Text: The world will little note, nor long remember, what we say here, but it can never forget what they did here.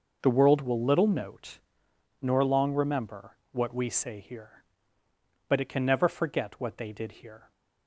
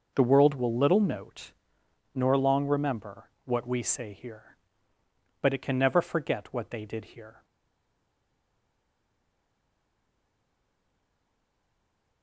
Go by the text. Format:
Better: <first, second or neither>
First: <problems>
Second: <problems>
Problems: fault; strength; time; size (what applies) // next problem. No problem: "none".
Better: first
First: none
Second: stays silent after the last word; strong; from 7.4 s on; 4.8 s long